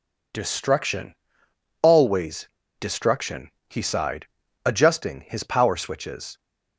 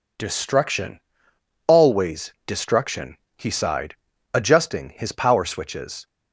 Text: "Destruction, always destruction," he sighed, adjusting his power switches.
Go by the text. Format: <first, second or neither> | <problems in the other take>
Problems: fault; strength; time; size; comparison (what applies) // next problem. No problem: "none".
second | pauses between "always" and "destruction"; slight; at 2.4 s; 0.32 s long